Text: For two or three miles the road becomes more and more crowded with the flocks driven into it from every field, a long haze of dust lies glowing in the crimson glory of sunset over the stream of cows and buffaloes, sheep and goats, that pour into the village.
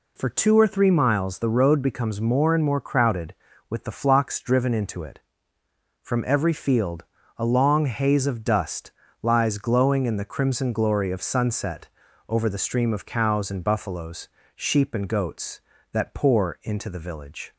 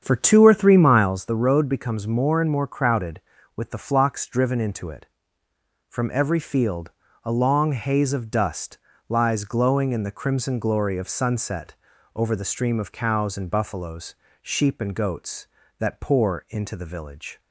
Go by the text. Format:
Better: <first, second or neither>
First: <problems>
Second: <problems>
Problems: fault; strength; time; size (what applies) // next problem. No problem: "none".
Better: first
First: pauses between "dust" and "lies"; slight; at 8.9 s; 0.30 s long // pauses between "sunset" and "over"; at 11.8 s; 0.42 s long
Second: starts louder than the rest; strong; until 1.2 s; 8 dB // pauses between "dust" and "lies"; slight; at 8.7 s; 0.30 s long // pauses between "sunset" and "over"; at 11.7 s; 0.42 s long